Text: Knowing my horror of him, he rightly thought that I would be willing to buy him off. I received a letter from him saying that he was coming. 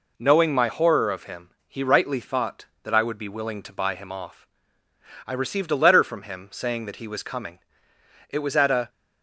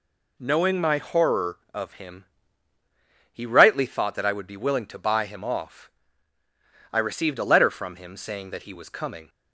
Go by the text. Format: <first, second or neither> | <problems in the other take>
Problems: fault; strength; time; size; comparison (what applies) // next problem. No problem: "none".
second | goes on to say "It was at a"; from 8.2 s on; 0.60 s long